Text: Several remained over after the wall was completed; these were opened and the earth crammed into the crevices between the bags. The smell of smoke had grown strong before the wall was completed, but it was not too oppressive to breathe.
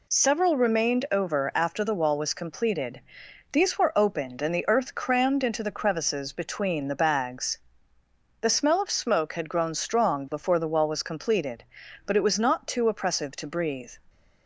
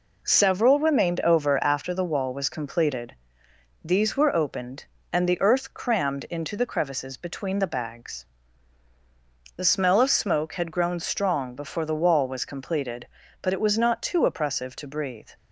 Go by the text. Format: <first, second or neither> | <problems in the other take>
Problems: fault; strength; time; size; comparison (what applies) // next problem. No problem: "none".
neither | none